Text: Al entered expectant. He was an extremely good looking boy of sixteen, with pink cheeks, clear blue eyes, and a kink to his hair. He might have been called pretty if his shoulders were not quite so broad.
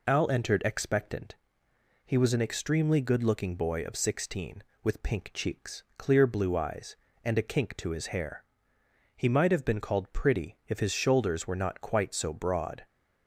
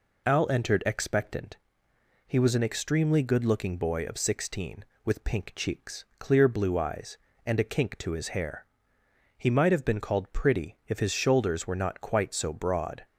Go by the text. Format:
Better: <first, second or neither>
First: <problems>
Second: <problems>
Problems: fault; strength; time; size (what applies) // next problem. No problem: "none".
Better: neither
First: none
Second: none